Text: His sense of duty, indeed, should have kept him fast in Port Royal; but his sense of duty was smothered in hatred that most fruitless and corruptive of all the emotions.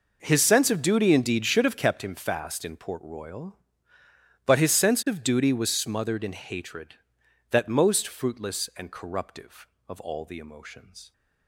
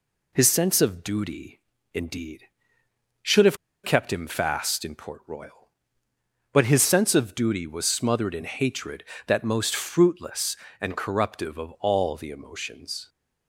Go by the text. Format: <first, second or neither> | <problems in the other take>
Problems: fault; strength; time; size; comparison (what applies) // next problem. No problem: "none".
first | pauses between "have" and "kept"; slight; at 3.5 s; 0.27 s long